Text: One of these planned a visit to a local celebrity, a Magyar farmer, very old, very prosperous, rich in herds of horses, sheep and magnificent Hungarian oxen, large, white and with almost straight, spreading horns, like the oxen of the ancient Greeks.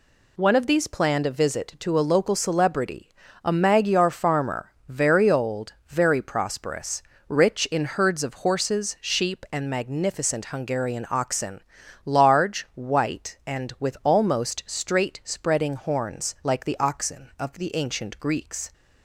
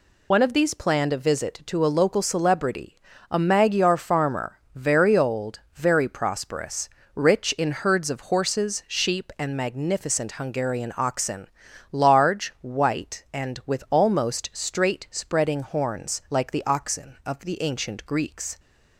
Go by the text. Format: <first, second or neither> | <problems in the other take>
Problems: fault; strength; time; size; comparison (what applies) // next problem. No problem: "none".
first | loses the start of "One"; at 0.3 s; 70 ms